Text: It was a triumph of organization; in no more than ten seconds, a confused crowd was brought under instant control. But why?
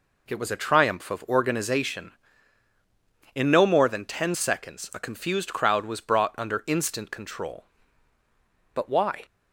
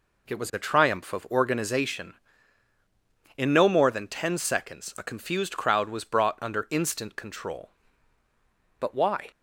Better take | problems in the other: neither | none

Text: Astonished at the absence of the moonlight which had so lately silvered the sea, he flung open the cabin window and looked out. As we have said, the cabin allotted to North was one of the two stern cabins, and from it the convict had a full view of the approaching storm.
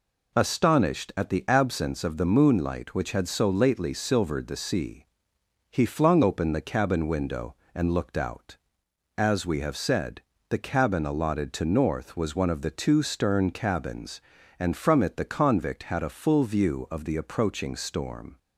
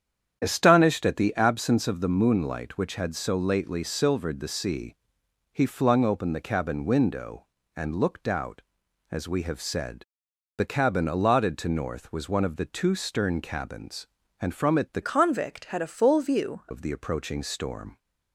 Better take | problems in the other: first | starts louder than the rest; strong; until 1.4 s; 8.5 dB // changes voice from "convict" to "view"; from 15.0 to 16.6 s; 1.6 s long

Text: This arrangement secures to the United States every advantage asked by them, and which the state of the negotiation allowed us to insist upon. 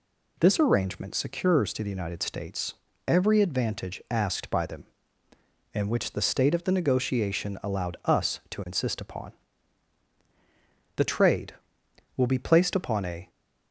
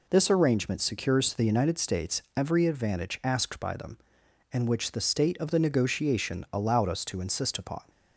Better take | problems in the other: second | pauses between "States" and "every"; slight; at 2.7 s; 0.34 s long // goes on to say "The trade will be placed upon a"; strong; from 10.9 s on; 2.3 s long

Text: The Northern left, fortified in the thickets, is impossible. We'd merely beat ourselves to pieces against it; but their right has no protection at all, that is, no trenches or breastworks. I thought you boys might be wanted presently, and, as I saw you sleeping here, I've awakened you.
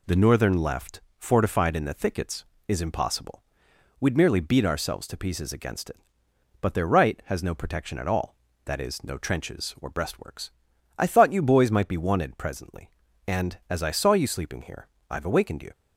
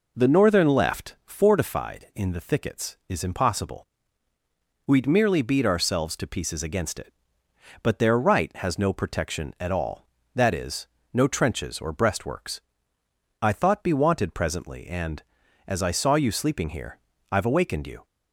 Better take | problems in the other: first | skips "you boys might"; at 13.8 s

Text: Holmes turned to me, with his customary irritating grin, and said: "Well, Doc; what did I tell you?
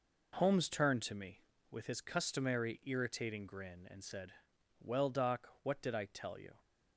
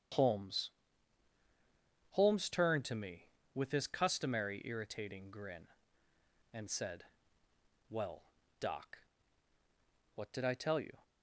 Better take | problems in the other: first | starts louder than the rest; strong; until 2.5 s; 8 dB // says "Holmes" twice; at 2.1 s

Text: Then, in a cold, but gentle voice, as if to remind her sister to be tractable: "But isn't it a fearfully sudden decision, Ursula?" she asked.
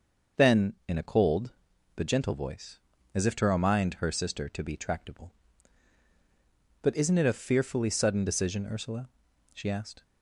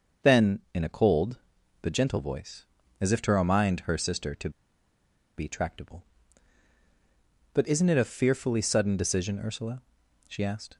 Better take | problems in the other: first | starts louder than the rest; until 1.3 s; 6.5 dB; also in the first // pauses between "to" and "be"; noticeable; at 4.4 s; 0.88 s long

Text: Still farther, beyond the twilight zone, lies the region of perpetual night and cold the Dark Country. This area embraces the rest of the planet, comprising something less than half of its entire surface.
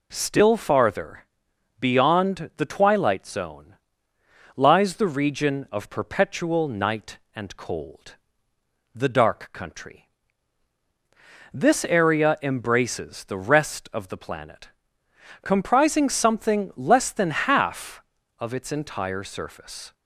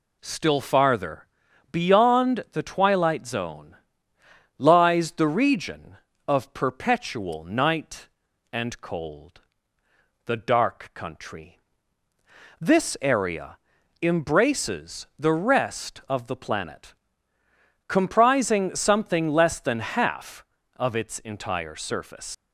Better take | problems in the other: first | pauses between "cold" and "the"; noticeable; at 9.4 s; 0.84 s long; noticeable in the first // pauses between "area" and "embraces"; noticeable; at 13.5 s; 0.46 s long // leaves "surface" unfinished; at 22.3 s; 145 ms

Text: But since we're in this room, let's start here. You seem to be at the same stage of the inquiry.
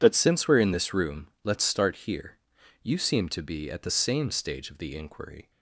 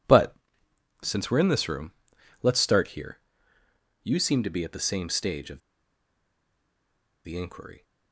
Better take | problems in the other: first | pauses between "But" and "since"; noticeable; at 0.3 s; 0.68 s long // pauses between "of" and "the"; strong; at 5.5 s; 1.6 s long

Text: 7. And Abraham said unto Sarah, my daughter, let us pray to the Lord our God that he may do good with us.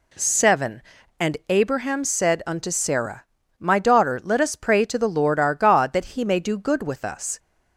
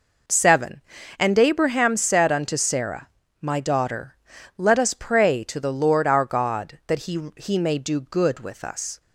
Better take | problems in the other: first | says "he" twice; at 7.3 s

